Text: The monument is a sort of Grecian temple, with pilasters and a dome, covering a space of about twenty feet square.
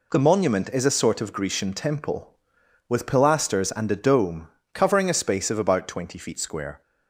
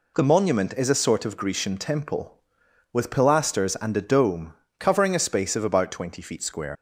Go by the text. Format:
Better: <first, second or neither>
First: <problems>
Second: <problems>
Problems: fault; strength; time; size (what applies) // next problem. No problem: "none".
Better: first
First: none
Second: leaves "square" unfinished; at 6.7 s; 90 ms